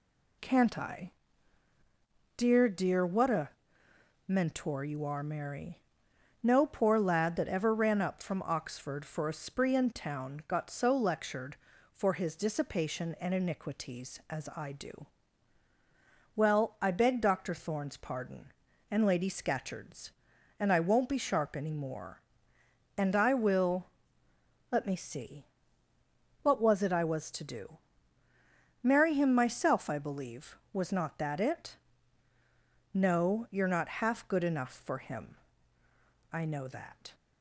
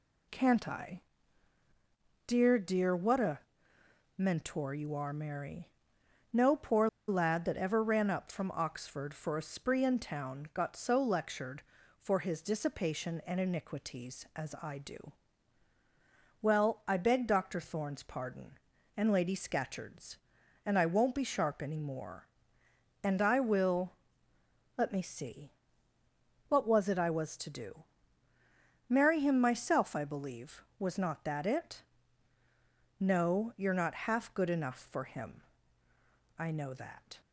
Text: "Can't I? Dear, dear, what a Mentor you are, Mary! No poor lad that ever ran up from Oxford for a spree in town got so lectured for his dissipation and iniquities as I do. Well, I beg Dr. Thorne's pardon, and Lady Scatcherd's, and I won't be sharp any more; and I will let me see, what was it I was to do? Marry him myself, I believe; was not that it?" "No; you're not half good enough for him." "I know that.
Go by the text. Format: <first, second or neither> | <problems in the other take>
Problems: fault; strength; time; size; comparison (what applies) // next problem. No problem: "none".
first | pauses between "a" and "Mentor"; noticeable; at 3.4 s; 0.80 s long; noticeable in the first // pauses between "poor" and "lad"; slight; at 6.8 s; 0.19 s long // pauses between "will" and "let"; noticeable; at 23.9 s; 0.84 s long; noticeable in the first